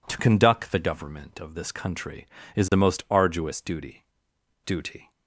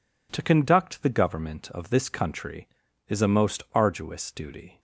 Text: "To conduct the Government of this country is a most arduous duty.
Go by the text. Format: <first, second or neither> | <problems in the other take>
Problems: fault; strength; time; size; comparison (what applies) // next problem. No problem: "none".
second | says "duty" twice; at 4.6 s